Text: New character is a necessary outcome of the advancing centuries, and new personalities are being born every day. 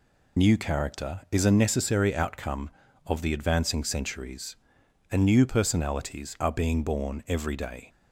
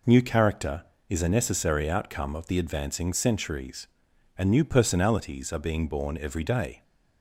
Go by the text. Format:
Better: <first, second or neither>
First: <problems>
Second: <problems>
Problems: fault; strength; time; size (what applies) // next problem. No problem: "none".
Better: second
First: loses the start of "New"; at 0.3 s; 40 ms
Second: none